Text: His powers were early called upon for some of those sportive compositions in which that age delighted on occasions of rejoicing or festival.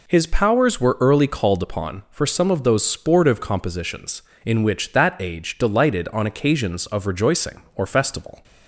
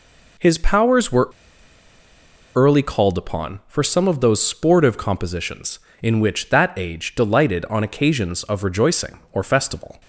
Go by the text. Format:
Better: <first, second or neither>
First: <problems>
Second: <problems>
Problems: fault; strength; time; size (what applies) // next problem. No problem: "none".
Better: first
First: none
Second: pauses between "were" and "early"; strong; at 1.2 s; 1.2 s long